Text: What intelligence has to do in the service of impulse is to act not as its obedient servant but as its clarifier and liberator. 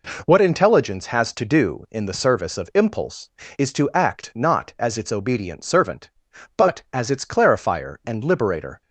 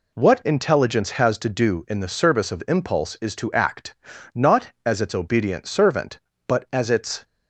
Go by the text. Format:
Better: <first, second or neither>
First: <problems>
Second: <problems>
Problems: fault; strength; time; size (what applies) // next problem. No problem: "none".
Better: first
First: none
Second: pauses between "act" and "not"; at 3.9 s; 0.40 s long // stops before "clarifier and liberator"; at 7.2 s